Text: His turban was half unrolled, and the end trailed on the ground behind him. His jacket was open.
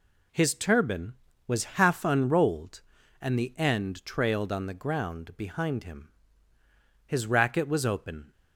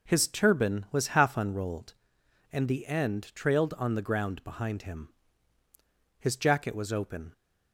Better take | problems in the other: second | says "racket" for "jacket"; at 7.2 s

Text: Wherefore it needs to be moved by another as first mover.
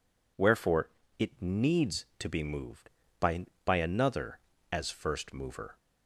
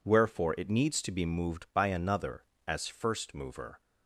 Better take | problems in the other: second | pauses between "Wherefore" and "it"; slight; at 0.8 s; 0.32 s long // says "by" twice; at 3.6 s

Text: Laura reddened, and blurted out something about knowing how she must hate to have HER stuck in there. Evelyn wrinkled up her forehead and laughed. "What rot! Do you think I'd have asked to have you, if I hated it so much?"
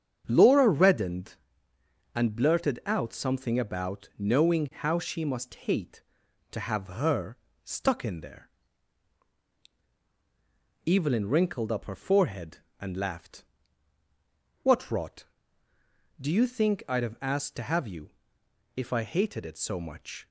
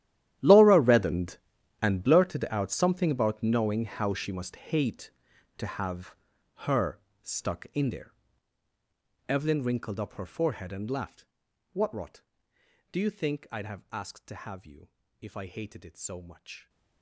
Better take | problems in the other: first | gets quieter; strong; throughout; 19 dB // starts louder than the rest; strong; until 1.8 s; 12.5 dB; strong in the first // pauses between "have" and "HER"; at 6.1 s; 0.40 s long // pauses between "HER" and "stuck"; slight; at 6.9 s; 0.24 s long; slight in the first

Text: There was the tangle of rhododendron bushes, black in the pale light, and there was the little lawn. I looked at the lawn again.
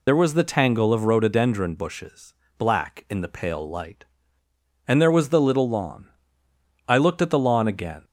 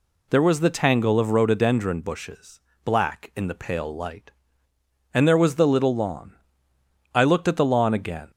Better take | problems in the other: second | loses the start of "There"; at 0.0 s; 35 ms

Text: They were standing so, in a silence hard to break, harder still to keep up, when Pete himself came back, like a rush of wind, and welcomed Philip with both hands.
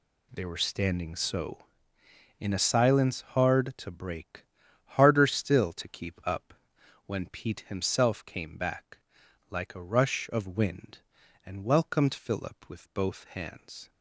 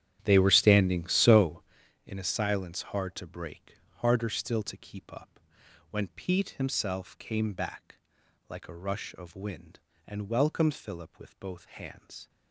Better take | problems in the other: first | starts louder than the rest; strong; until 1.8 s; 11 dB

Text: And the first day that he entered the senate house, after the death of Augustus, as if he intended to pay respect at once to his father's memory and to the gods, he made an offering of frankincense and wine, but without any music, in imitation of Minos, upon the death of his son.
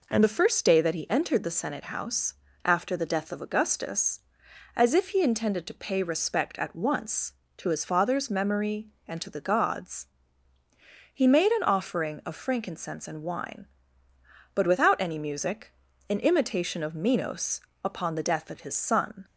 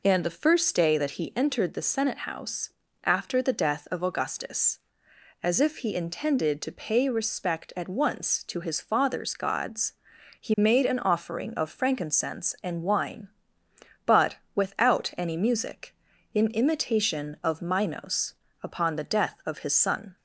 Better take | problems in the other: first | skips "memory and to the"; at 9.3 s // pauses between "but" and "without"; slight; at 14.3 s; 0.18 s long

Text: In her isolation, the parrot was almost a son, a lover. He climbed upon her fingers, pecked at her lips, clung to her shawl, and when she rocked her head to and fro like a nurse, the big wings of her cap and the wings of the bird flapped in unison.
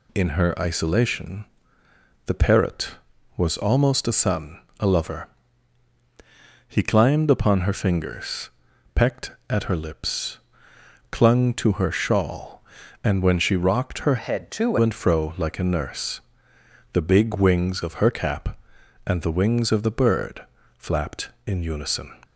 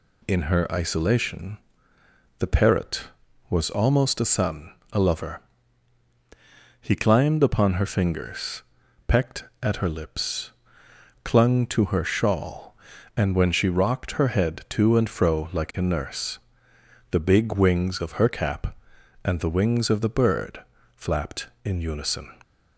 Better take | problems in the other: second | changes voice from "head" to "to"; from 14.1 to 14.7 s; 0.6 s long // pauses between "bird" and "flapped"; slight; at 20.4 s; 0.32 s long; slight in the second

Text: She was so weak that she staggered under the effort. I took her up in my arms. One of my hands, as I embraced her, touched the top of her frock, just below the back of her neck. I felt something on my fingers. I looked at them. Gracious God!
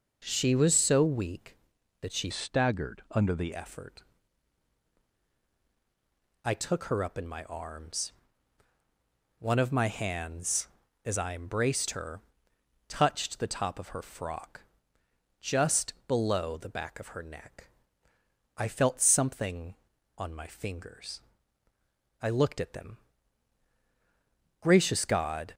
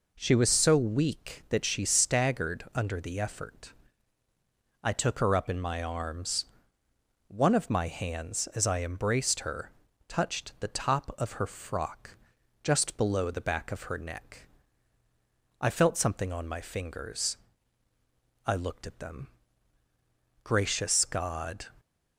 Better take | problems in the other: second | changes voice from "staggered" to "the"; from 2.3 to 3.5 s; 1.2 s long // pauses between "just" and "below"; slight; at 15.9 s; 0.16 s long

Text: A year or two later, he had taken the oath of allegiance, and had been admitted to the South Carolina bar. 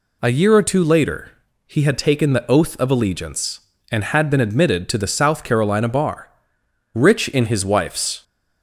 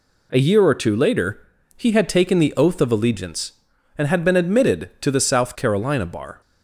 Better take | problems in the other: second | goes on to say "Rich in his wife's"; noticeable; from 6.9 s on; 1.3 s long

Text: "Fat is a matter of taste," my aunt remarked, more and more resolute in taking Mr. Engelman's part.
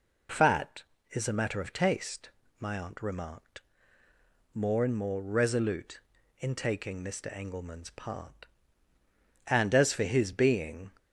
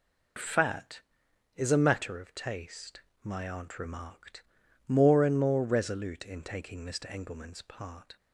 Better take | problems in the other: second | goes on to say "And as for his being"; from 9.4 s on; 1.4 s long

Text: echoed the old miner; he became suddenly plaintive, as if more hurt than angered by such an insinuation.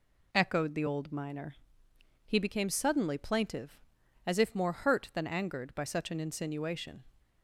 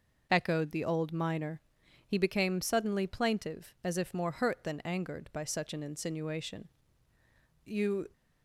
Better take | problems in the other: first | goes on to say "You"; slight; from 7.6 s on; 0.44 s long

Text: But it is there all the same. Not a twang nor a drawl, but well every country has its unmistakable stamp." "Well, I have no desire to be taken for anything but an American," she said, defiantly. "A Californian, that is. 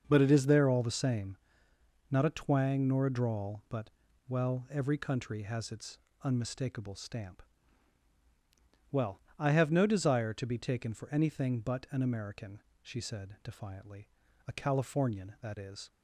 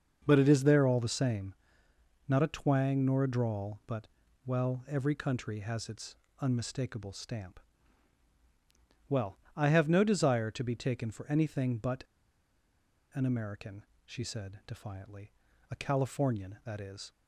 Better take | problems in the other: first | starts louder than the rest; until 1.2 s; 6 dB; also in the first // pauses between "but" and "well"; at 4.0 s; 0.40 s long; also in the first // pauses between "its" and "unmistakable"; slight; at 6.1 s; 0.24 s long; slight in the first // pauses between "but" and "an"; at 12.0 s; 1.0 s long

